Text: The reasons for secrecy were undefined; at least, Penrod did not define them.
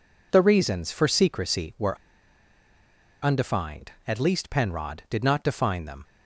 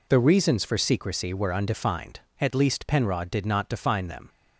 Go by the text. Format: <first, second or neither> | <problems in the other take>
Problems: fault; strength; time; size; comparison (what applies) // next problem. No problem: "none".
second | pauses between "were" and "undefined"; strong; at 1.9 s; 1.2 s long